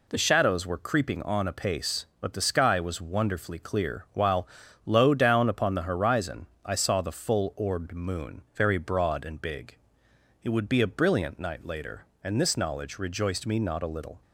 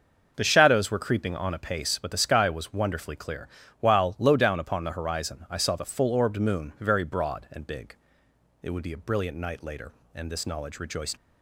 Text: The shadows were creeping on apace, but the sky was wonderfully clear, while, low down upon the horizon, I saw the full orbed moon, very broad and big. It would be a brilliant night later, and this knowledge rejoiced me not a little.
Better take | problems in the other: first | starts louder than the rest; until 1.3 s; 6.5 dB // stops before "me not a little"; at 11.1 s

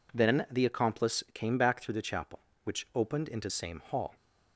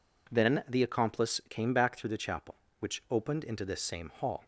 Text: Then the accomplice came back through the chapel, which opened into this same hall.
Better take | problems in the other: second | skips "this"; at 3.5 s

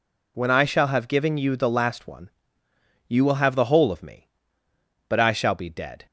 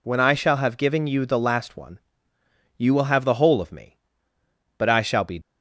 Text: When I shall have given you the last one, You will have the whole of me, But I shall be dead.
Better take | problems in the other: first | stops before "dead"; at 5.4 s

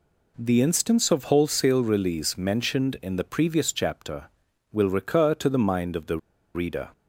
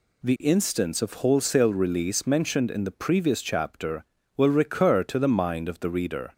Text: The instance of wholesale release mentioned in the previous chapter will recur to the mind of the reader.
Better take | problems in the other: second | pauses between "the" and "reader"; at 6.1 s; 0.37 s long

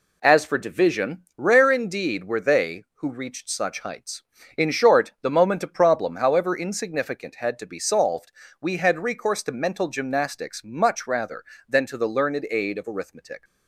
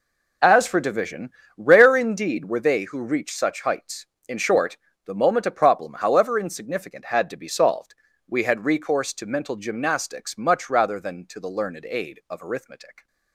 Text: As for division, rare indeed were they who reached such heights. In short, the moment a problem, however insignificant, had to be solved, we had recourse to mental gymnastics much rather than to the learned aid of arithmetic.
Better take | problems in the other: neither | none

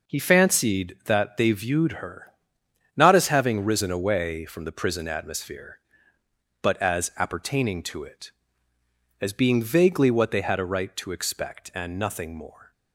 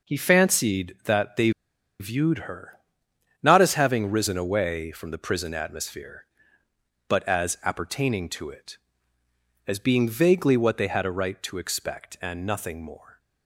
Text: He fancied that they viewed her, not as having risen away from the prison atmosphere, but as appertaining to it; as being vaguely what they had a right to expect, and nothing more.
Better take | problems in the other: first | pauses between "they" and "viewed"; noticeable; at 1.4 s; 0.49 s long

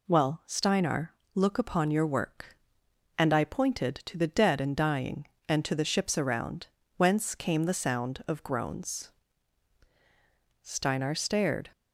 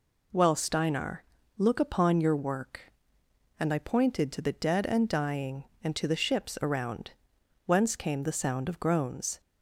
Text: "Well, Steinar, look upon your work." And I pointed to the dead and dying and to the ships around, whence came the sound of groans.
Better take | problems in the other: second | goes on to say "Steinar stared"; noticeable; from 10.6 s on; 1.1 s long

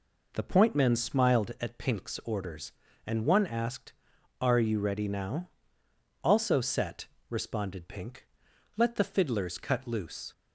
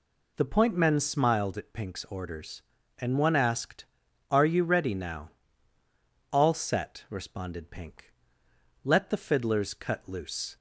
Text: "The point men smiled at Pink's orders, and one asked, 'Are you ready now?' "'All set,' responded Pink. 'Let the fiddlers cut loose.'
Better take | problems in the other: second | says "Also" for "All"; at 6.2 s

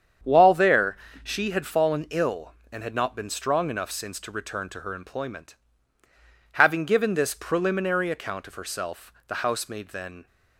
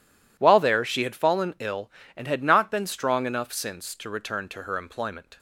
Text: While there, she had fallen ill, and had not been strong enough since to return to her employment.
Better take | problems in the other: second | starts louder than the rest; strong; until 1.5 s; 8 dB // goes on to say "Having given this preliminary account of herself the housemaid then"; strong; from 6.5 s on; 3.7 s long

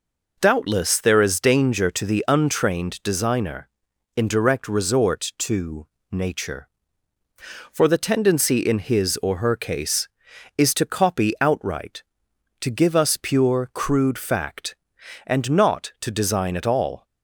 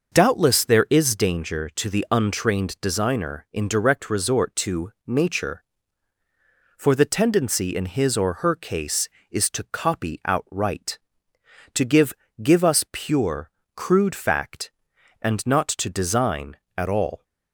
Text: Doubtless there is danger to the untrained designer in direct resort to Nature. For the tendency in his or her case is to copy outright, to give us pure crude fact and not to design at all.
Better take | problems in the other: first | pauses between "to" and "Nature"; slight; at 4.9 s; 0.16 s long; slight in the first // says "give" twice; at 12.4 s // pauses between "pure" and "crude"; slight; at 13.4 s; 0.26 s long

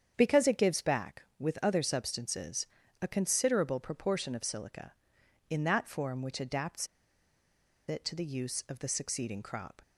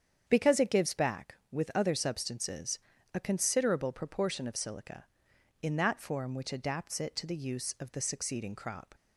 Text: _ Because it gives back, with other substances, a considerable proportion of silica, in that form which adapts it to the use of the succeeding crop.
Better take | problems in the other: second | starts louder than the rest; strong; until 1.1 s; 8 dB; strong in the second // pauses between "adapts" and "it"; at 6.8 s; 1.0 s long

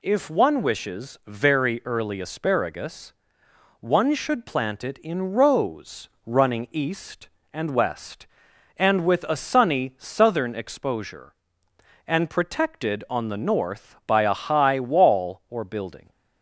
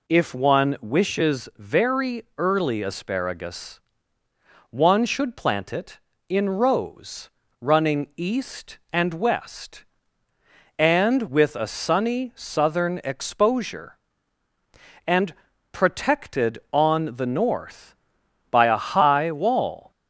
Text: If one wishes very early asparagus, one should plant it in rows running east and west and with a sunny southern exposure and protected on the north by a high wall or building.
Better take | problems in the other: first | pauses between "rows" and "running"; slight; at 7.2 s; 0.32 s long; slight in the first // pauses between "and" and "protected"; at 15.3 s; 0.40 s long // stops before "or building"; at 19.9 s

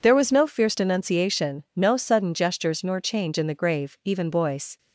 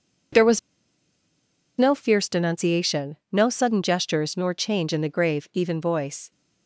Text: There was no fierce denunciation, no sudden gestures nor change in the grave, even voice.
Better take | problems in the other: first | pauses between "was" and "no"; at 0.5 s; 1.1 s long

